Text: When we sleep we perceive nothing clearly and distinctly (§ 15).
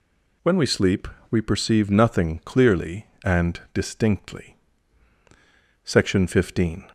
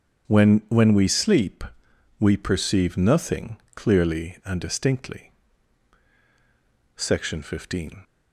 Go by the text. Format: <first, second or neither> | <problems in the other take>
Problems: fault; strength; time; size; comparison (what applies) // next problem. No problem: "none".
first | starts louder than the rest; strong; until 1.3 s; 8 dB // says "When" twice; at 0.6 s // pauses between "sleep" and "we"; noticeable; at 1.6 s; 0.52 s long; slight in the first // pauses between "nothing" and "clearly"; slight; at 3.5 s; 0.18 s long